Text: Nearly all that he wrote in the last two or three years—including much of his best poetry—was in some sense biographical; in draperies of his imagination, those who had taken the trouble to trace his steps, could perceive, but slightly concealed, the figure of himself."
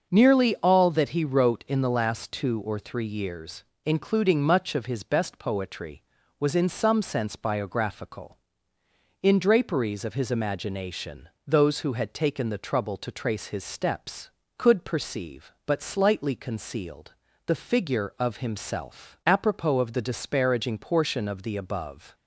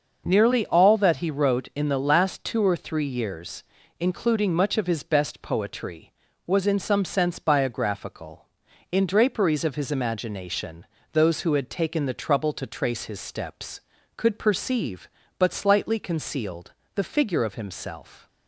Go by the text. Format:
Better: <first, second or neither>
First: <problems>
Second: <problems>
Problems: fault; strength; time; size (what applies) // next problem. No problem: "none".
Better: second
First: starts louder than the rest; until 1.1 s; 6 dB // goes on to say "Apropos of the disparaging portion of the above"; strong; from 19.2 s on; 2.8 s long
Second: starts louder than the rest; noticeable; until 1.2 s; 6 dB